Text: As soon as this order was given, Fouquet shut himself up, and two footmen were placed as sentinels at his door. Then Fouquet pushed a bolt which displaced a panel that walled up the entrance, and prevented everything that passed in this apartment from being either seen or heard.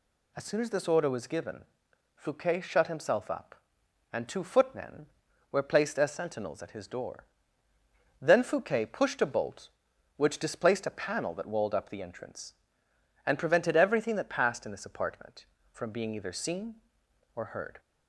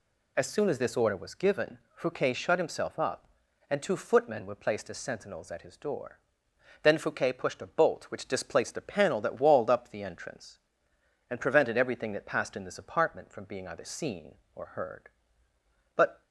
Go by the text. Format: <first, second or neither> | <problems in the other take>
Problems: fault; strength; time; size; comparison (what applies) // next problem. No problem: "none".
first | goes on to say "But"; slight; from 15.9 s on; 0.28 s long